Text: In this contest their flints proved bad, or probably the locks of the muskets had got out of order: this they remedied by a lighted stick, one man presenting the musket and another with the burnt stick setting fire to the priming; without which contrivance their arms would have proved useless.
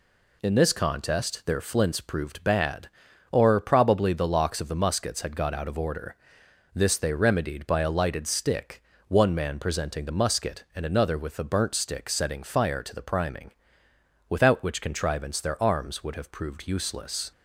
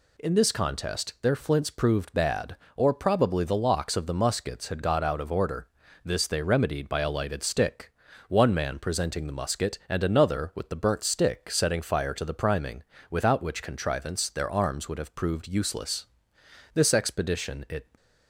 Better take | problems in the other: first | goes on to say "This expedition it"; noticeable; from 16.7 s on; 1.1 s long

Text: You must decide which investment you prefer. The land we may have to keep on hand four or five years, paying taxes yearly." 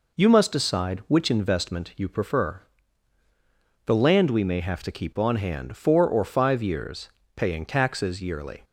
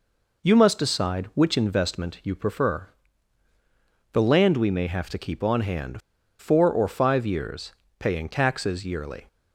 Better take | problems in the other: first | pauses between "hand" and "four"; at 5.9 s; 0.39 s long

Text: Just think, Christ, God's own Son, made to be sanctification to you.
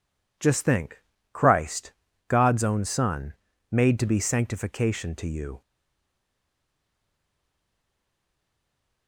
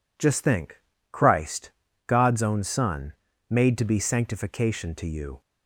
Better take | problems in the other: second | stays silent after the last word; strong; from 5.6 s on; 3.4 s long

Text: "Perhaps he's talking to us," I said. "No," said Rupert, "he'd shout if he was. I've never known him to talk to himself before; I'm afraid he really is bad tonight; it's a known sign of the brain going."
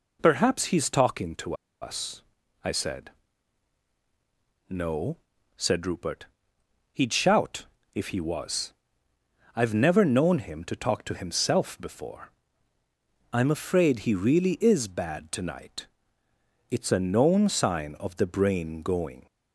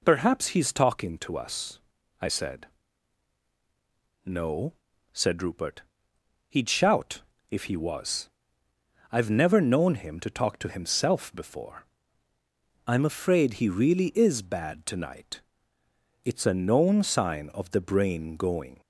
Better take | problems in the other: second | pauses between "to" and "us"; slight; at 1.5 s; 0.27 s long // pauses between "shout" and "if"; slight; at 7.6 s; 0.30 s long; slight in the second

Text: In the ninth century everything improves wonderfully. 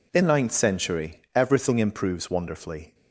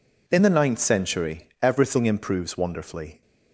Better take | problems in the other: second | skips "the"; at 0.2 s

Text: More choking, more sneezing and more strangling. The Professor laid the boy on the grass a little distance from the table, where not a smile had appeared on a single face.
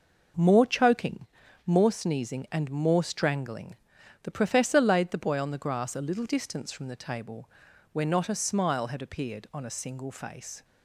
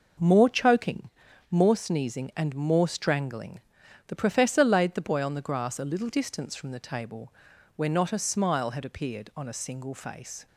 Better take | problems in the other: neither | none

